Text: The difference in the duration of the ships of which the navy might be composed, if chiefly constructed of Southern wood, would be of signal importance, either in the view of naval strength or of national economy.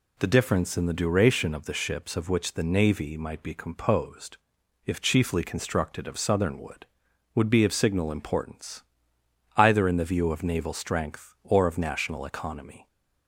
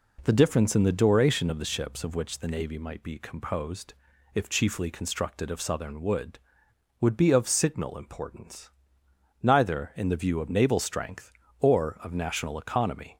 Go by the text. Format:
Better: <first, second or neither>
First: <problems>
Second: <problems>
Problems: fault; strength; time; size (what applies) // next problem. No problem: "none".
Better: first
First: none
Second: says "neither" for "either"; at 9.4 s